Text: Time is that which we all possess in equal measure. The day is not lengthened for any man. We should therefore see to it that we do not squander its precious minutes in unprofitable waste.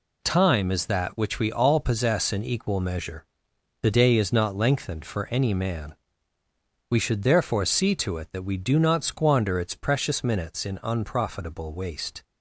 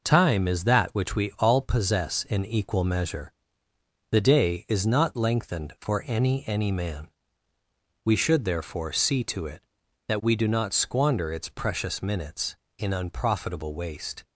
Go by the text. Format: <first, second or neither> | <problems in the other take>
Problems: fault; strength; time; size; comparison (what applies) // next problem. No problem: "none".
first | says "any" twice; at 6.4 s